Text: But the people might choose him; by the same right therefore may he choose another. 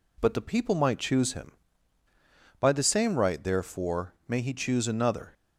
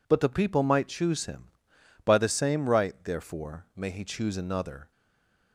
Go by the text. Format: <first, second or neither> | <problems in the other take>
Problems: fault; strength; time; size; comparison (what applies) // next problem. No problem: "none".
first | stays silent after the last word; slight; from 4.9 s on; 0.6 s long